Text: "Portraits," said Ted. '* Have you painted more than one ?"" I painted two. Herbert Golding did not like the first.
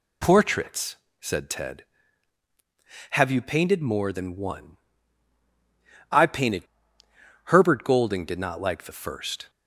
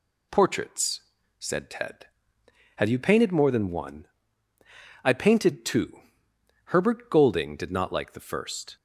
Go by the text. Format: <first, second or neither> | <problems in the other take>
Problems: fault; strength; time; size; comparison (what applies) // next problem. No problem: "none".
second | skips "two"; at 7.0 s